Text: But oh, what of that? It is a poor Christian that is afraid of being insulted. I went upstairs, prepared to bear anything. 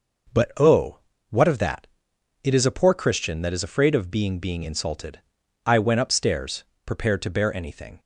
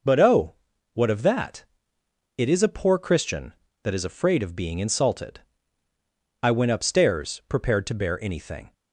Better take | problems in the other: second | says "being" twice; at 4.3 s

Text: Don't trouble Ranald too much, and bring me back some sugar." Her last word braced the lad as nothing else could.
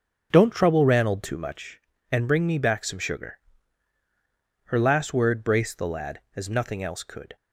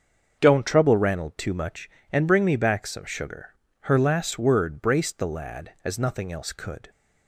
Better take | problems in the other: neither | starts louder than the rest; the same in both

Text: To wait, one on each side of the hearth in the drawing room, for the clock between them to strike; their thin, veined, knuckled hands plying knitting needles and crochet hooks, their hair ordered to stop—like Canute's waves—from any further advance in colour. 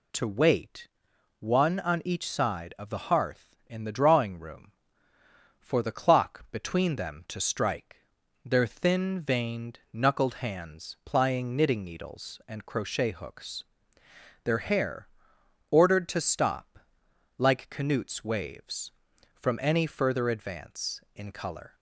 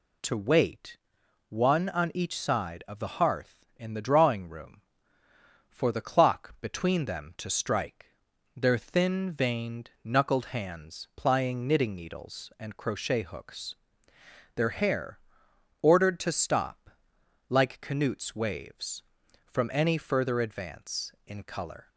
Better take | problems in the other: neither | pauses between "hair" and "ordered"; noticeable; the same in both

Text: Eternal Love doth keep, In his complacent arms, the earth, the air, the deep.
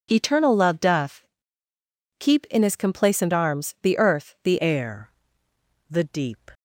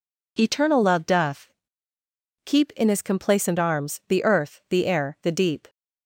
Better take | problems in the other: second | pauses between "doth" and "keep"; noticeable; at 1.2 s; 0.96 s long; noticeable in the second // changes voice at "air"; from 4.5 s on; 2.0 s long

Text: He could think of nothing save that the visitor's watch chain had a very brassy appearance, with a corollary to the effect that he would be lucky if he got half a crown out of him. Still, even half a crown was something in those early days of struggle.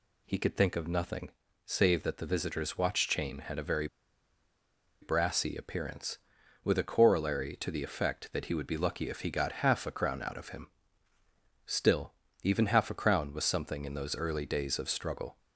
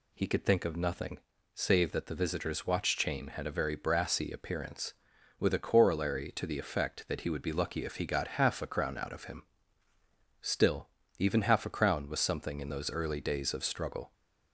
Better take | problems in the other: second | pauses between "nothing" and "save"; at 1.2 s; 0.38 s long; also in the second // pauses between "very" and "brassy"; at 3.8 s; 1.1 s long

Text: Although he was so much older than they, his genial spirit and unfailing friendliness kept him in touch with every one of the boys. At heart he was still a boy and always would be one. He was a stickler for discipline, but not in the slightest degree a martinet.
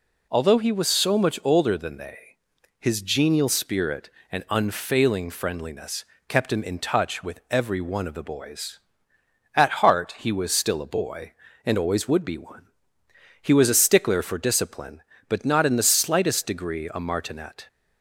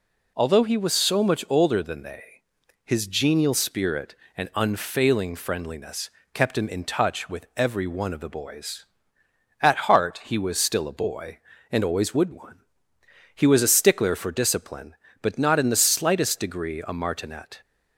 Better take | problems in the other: first | pauses between "friendliness" and "kept"; slight; at 6.0 s; 0.24 s long; slight in the first // skips "be"; at 12.3 s

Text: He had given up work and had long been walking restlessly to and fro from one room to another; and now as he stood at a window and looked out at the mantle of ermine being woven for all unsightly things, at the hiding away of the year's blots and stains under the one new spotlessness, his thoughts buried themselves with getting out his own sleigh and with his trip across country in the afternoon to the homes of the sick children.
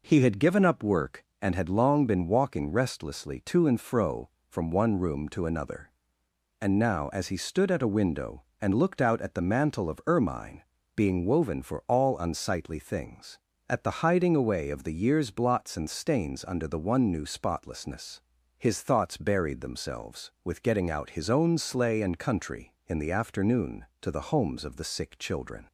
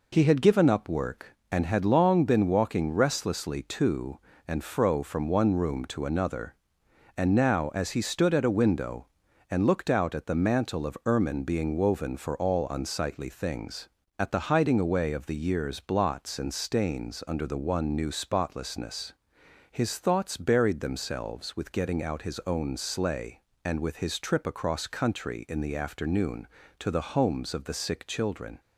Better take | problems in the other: second | pauses between "ermine" and "being"; slight; at 10.6 s; 0.34 s long // skips "with his trip across"; at 22.1 s

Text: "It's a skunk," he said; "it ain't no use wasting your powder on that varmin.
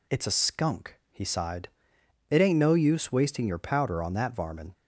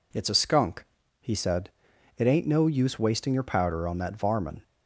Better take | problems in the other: second | says "sighed" for "said"; at 1.2 s

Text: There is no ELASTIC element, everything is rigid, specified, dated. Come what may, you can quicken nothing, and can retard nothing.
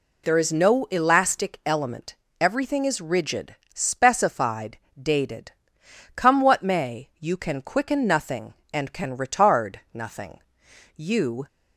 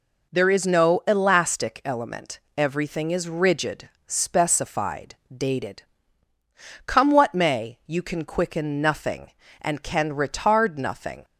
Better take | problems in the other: second | pauses between "retard" and "nothing"; slight; at 9.7 s; 0.16 s long // goes on to say "You"; from 10.9 s on; 0.50 s long

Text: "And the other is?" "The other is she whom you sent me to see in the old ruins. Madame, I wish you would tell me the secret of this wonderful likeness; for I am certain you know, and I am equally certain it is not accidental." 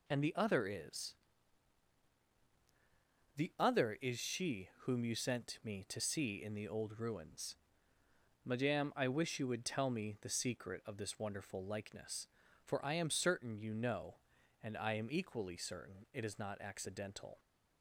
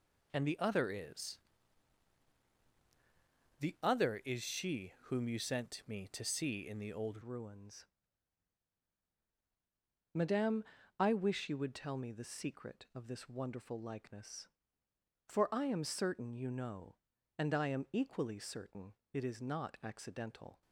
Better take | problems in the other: first | changes voice at "ruins"; from 7.2 s on; 13.4 s long // pauses between "certain" and "it"; slight; at 18.9 s; 0.20 s long

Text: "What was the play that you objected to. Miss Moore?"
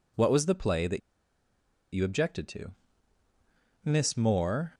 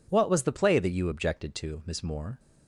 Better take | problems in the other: second | pauses between "that" and "you"; noticeable; at 0.9 s; 0.93 s long

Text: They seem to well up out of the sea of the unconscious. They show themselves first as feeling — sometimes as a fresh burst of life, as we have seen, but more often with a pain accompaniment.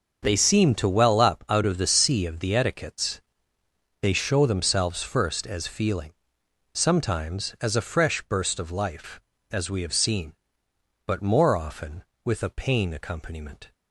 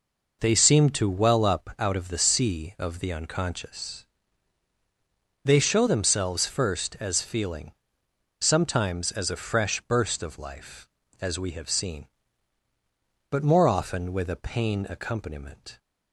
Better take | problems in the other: second | starts louder than the rest; until 1.2 s; 6 dB // says "etiquettes" for "unconscious"; at 2.5 s

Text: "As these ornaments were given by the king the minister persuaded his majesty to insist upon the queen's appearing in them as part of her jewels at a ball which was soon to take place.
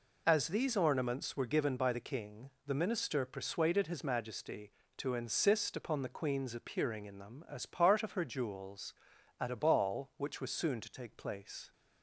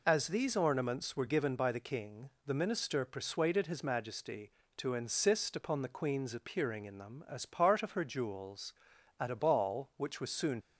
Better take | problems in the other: first | pauses between "king" and "the"; slight; at 2.2 s; 0.16 s long; slight in the first // stops before "to take place"; at 10.6 s

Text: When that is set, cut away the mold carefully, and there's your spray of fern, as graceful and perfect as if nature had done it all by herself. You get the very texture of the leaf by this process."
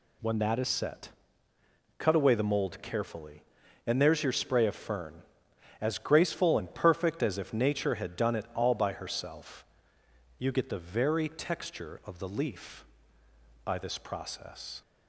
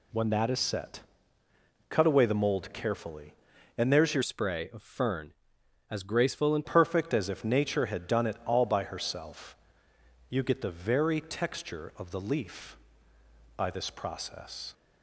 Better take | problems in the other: first | changes voice from "spray" to "and"; from 4.2 to 6.6 s; 2.4 s long

